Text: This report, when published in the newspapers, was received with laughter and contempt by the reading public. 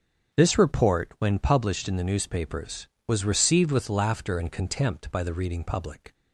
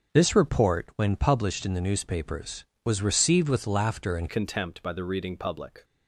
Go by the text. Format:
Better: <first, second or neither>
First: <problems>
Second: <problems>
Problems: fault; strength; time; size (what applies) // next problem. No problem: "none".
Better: first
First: starts louder than the rest; strong; until 1.4 s; 7.5 dB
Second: starts louder than the rest; until 1.1 s; 6.5 dB // changes voice at "contempt"; from 4.2 s on; 1.6 s long